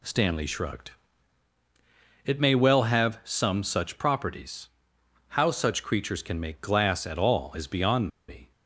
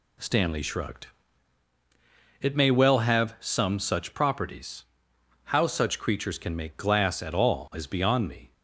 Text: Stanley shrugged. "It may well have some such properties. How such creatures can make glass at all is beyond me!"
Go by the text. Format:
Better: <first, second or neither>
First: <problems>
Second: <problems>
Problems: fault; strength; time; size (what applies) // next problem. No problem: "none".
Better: second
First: pauses between "beyond" and "me"; slight; at 8.0 s; 0.19 s long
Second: none